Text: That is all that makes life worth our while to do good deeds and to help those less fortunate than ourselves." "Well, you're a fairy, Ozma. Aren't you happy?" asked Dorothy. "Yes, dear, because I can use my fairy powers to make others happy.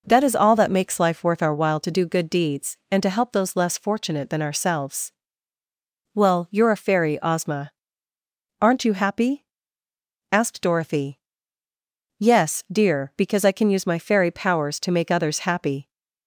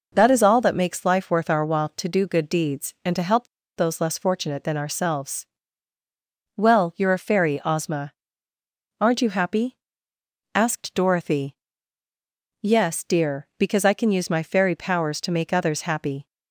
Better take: first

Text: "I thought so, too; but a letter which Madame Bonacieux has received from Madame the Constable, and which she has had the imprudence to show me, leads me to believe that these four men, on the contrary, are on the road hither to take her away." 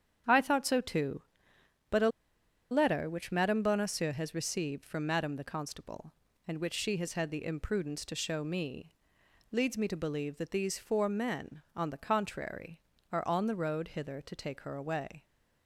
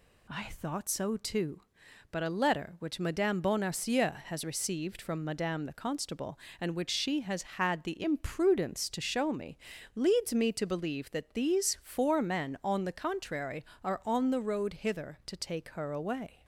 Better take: second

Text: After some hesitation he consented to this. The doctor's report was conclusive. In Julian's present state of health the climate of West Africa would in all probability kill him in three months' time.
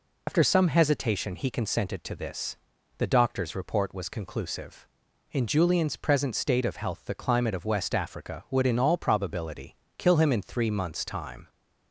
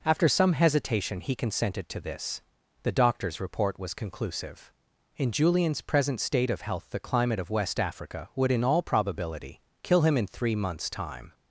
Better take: second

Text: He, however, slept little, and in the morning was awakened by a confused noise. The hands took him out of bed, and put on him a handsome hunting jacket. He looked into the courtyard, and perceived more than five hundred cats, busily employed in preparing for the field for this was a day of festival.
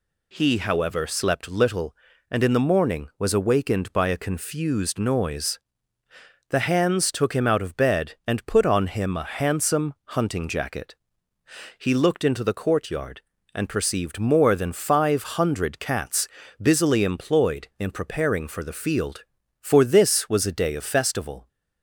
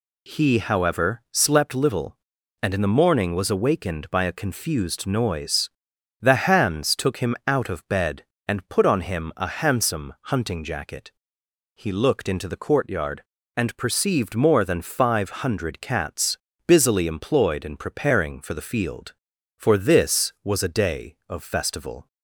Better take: neither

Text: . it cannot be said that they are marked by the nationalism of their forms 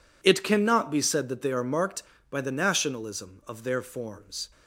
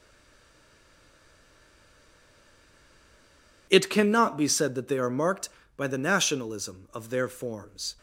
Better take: first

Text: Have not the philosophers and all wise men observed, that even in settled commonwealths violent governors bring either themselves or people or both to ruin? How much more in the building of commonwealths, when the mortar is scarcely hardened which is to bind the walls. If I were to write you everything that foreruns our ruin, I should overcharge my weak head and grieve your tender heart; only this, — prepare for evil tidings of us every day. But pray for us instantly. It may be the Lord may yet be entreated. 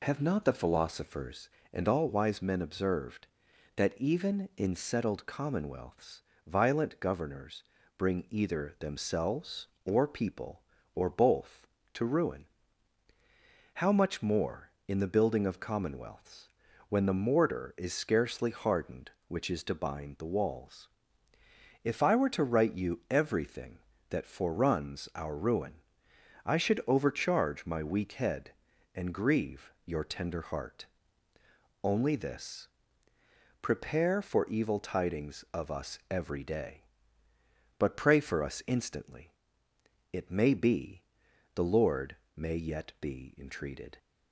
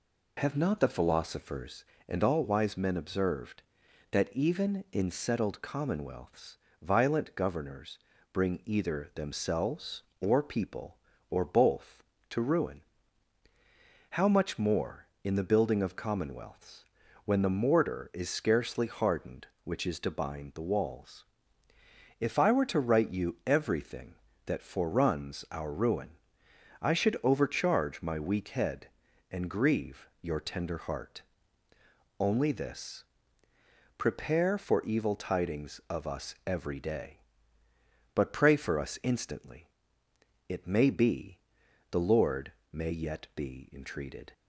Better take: neither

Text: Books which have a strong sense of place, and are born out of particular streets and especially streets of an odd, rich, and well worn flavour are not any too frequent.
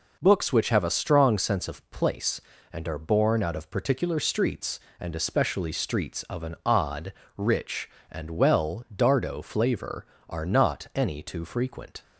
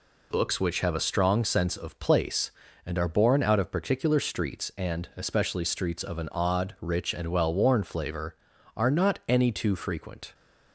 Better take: second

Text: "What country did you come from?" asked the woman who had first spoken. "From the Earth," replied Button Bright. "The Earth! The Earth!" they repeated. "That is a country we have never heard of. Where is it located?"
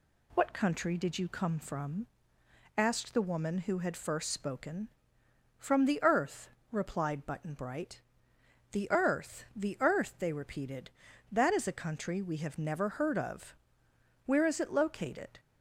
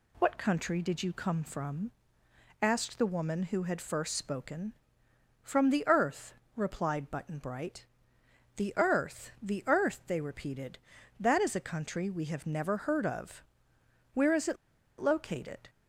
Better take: first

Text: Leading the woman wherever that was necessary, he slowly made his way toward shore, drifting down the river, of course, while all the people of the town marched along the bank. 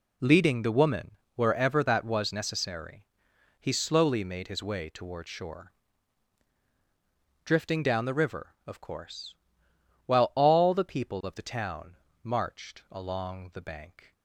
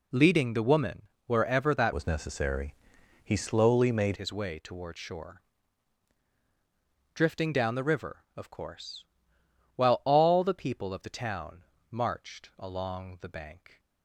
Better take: first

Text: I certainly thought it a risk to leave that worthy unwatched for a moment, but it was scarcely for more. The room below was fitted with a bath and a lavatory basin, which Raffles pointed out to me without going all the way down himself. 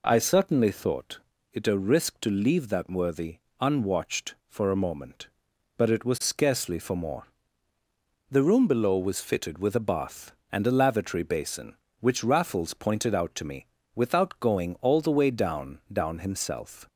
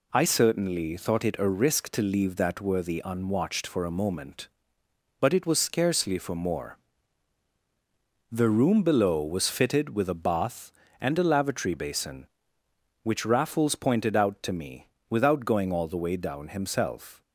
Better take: second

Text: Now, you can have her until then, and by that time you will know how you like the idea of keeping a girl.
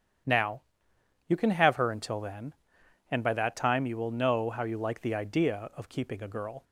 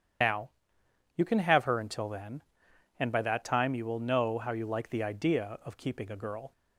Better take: first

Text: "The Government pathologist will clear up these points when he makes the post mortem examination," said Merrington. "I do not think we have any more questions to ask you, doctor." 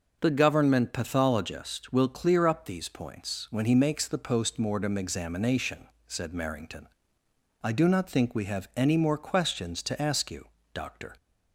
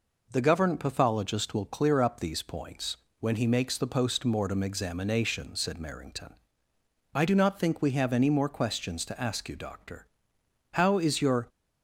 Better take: first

